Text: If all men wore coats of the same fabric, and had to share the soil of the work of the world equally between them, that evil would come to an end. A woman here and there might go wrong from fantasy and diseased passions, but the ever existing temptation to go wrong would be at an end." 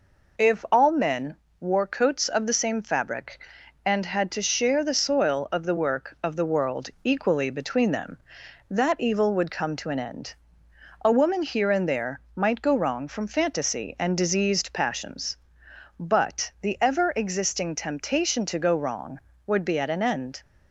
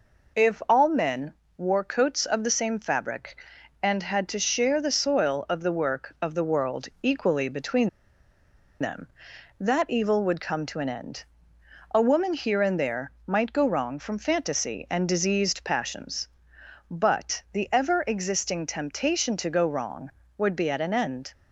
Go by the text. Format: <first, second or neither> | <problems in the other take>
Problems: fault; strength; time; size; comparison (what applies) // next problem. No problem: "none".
first | pauses between "men" and "wore"; slight; at 1.3 s; 0.24 s long; slight in the first // pauses between "between" and "them"; noticeable; at 7.8 s; 0.91 s long